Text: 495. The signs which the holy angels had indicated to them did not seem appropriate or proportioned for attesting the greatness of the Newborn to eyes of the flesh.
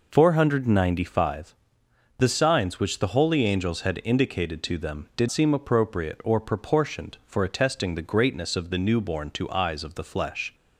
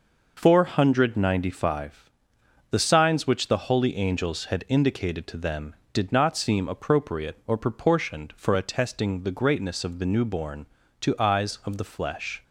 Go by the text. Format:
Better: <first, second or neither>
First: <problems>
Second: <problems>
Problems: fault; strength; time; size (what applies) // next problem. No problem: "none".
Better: second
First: skips "not"; at 5.2 s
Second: none